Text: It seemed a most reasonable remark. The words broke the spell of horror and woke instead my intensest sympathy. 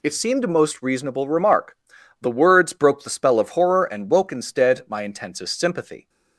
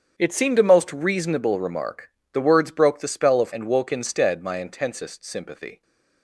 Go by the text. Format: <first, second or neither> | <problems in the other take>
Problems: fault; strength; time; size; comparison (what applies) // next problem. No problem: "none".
first | starts louder than the rest; strong; until 1.2 s; 7.5 dB // skips "horror"; at 3.5 s